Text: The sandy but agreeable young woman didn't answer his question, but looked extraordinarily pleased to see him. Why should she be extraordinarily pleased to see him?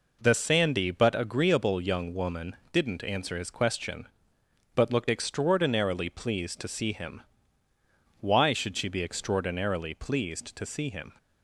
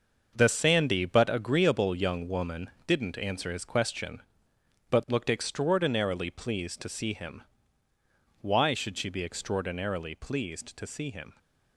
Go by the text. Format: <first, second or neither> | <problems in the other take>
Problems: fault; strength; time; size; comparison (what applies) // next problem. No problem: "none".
first | gets quieter; strong; throughout; 8.5 dB // pauses between "woman" and "didn't"; slight; at 2.7 s; 0.16 s long; slight in the first